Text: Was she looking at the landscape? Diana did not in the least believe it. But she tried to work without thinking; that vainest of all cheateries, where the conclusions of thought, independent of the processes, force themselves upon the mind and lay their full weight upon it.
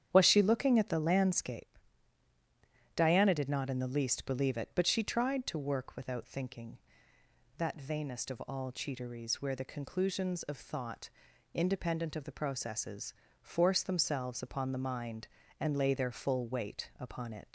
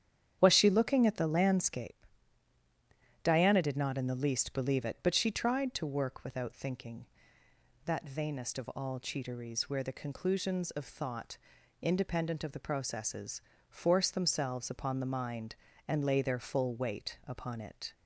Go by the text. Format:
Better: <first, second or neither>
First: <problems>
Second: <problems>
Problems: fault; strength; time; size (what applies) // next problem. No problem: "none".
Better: second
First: starts louder than the rest; strong; until 1.1 s; 9 dB // leaves "it" unfinished; at 17.4 s; 105 ms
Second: starts louder than the rest; strong; until 1.4 s; 9 dB